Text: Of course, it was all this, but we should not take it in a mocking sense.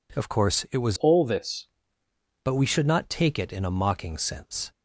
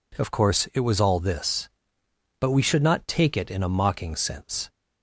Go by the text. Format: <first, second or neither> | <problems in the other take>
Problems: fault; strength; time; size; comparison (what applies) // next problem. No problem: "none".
second | changes voice from "all" to "this"; from 0.9 to 1.6 s; 0.7 s long